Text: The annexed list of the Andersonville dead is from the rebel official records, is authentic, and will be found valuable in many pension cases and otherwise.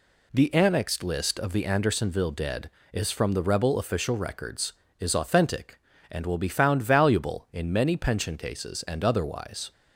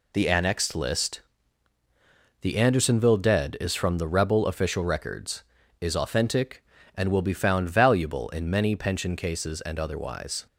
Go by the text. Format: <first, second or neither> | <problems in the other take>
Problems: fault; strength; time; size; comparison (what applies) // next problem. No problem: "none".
first | skips "of"; at 1.7 s